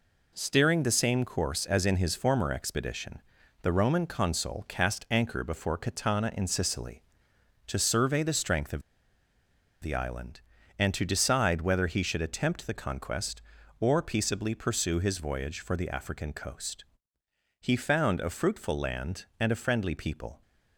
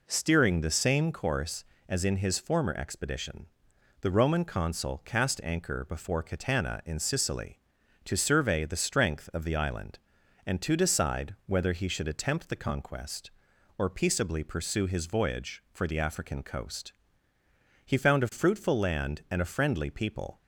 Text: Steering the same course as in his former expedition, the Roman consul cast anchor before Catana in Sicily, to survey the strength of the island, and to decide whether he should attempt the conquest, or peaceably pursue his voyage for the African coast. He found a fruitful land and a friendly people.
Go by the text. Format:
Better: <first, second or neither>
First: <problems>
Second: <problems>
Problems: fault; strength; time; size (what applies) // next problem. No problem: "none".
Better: second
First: pauses between "of" and "the"; at 8.8 s; 1.0 s long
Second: none